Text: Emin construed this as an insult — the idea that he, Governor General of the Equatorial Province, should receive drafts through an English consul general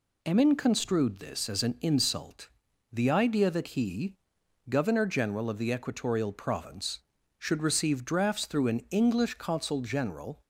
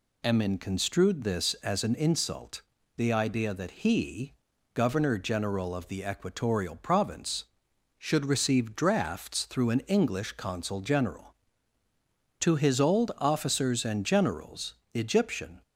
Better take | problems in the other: first | goes on to say "To his old officers and generals Egyptian"; strong; from 12.3 s on; 3.2 s long

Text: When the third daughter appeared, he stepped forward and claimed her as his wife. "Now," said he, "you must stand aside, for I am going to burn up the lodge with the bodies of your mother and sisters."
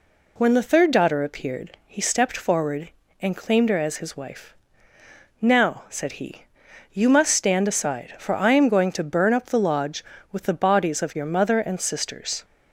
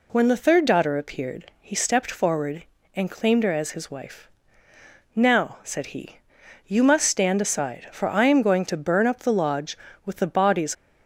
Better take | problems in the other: first | stops before "of your mother and sisters"; at 10.7 s

